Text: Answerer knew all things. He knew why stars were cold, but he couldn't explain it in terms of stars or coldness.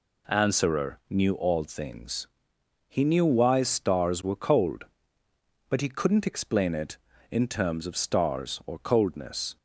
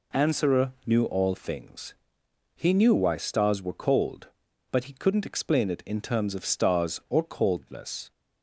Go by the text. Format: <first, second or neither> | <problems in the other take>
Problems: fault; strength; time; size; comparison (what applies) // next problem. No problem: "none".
neither | none